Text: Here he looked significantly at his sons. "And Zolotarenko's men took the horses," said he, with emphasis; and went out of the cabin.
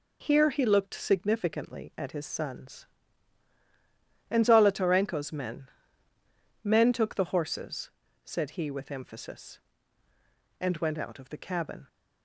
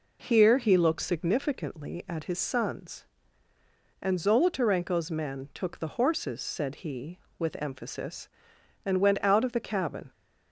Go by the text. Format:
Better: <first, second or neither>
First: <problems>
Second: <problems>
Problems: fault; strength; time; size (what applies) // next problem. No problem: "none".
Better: second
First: says "men" twice; at 6.6 s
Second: none